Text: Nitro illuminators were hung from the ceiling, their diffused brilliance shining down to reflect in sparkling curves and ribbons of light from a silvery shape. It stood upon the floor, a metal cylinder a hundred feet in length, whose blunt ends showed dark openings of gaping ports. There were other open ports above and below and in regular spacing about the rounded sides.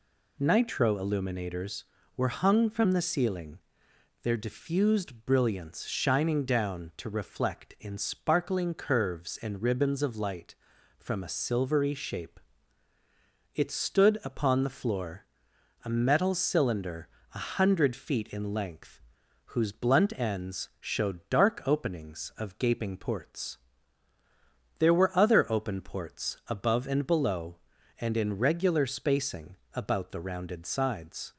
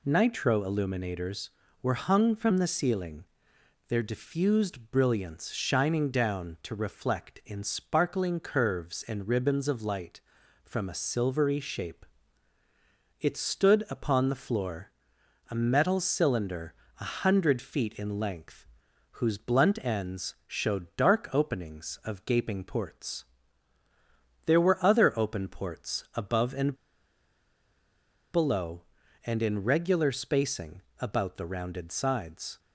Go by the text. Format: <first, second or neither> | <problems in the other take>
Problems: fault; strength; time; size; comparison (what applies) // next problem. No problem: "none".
first | pauses between "cylinder" and "a"; slight; at 16.7 s; 0.26 s long; slight in the first // pauses between "and" and "below"; strong; at 26.7 s; 1.6 s long // pauses between "spacing" and "about"; slight; at 30.8 s; 0.20 s long; slight in the first